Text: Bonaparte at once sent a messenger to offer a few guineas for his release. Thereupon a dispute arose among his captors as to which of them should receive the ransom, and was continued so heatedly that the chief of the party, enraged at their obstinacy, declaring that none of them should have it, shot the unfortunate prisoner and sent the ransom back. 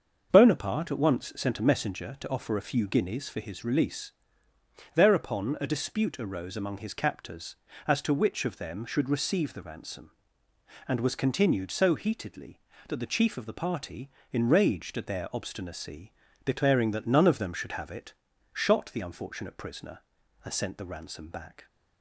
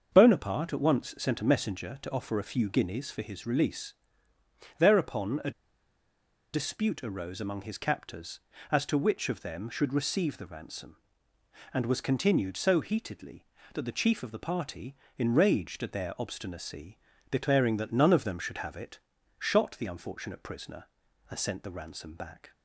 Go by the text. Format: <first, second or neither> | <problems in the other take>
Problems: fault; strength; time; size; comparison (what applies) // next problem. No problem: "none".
first | starts louder than the rest; until 1.1 s; 6.5 dB; also in the first // pauses between "a" and "dispute"; at 5.4 s; 1.0 s long